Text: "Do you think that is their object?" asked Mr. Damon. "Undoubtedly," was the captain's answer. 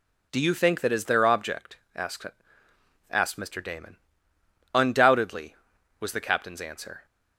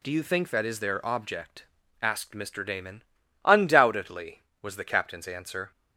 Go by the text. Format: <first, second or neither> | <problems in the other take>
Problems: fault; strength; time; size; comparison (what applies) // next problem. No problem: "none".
second | says "asked" twice; at 3.0 s